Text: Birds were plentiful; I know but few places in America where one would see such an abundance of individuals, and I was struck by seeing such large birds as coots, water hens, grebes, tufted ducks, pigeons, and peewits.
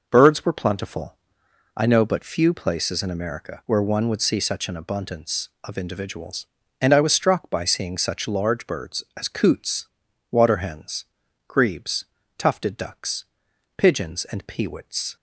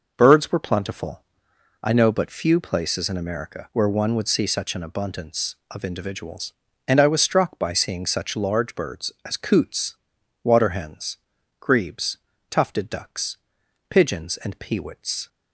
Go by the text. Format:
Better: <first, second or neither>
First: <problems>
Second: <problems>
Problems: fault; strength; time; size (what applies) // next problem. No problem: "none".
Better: neither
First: none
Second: none